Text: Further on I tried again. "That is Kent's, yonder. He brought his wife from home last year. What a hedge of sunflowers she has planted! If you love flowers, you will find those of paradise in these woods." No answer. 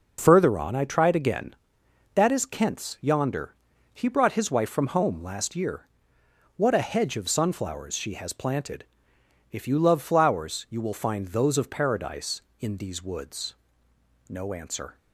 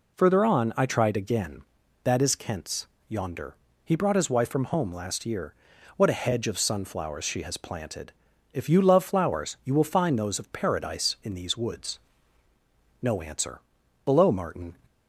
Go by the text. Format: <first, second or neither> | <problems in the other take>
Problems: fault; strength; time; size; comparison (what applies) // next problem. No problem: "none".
first | goes on to say "Below Martin"; noticeable; from 14.0 s on; 0.72 s long